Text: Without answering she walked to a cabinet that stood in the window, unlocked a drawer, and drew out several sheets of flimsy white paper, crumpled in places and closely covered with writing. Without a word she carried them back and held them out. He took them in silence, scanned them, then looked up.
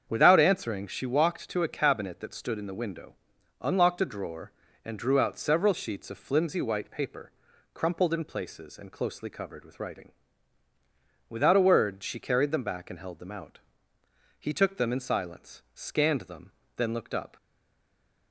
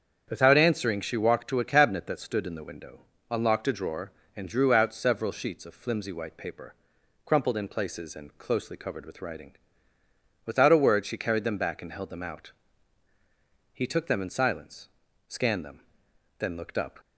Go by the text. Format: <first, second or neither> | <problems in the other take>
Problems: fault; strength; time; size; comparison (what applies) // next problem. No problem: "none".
second | starts louder than the rest; strong; until 1.0 s; 7.5 dB; strong in the second // stays silent after the last word; slight; from 17.3 s on; 1.0 s long